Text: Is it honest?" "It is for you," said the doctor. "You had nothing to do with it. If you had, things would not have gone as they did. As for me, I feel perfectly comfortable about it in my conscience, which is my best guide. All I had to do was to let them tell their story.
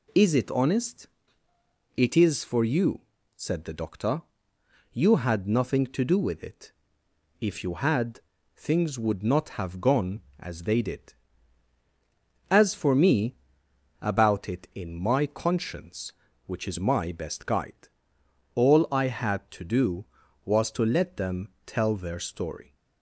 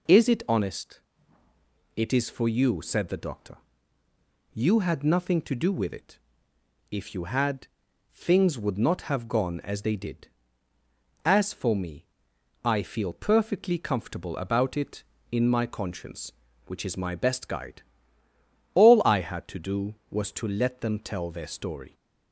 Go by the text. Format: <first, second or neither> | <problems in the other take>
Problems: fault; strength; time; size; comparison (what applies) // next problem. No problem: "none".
second | skips "I feel perfectly comfortable"; at 13.6 s // pauses between "them" and "tell"; slight; at 21.4 s; 0.16 s long